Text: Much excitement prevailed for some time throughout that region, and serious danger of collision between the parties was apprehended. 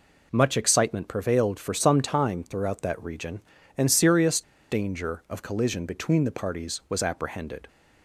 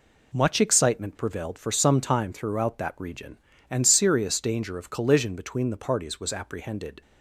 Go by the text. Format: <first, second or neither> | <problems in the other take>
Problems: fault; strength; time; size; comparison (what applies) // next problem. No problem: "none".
second | pauses between "serious" and "danger"; slight; at 4.4 s; 0.29 s long